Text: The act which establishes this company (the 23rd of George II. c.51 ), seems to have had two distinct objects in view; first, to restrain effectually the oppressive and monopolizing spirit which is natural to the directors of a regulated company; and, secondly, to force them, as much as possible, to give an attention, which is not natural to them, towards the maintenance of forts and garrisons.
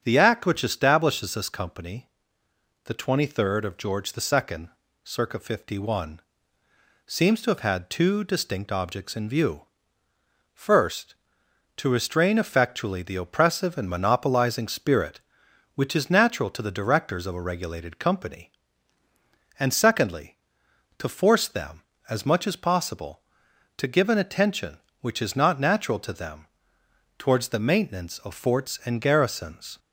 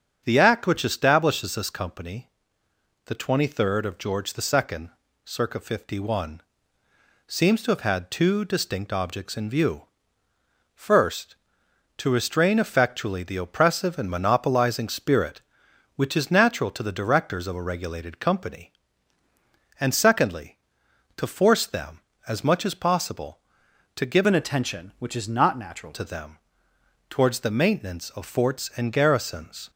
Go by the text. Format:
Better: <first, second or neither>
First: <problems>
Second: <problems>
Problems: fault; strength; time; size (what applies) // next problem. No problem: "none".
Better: first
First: starts louder than the rest; strong; until 1.0 s; 9 dB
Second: starts louder than the rest; strong; until 1.2 s; 9 dB // changes voice from "an" to "natural"; from 24.2 to 25.9 s; 1.7 s long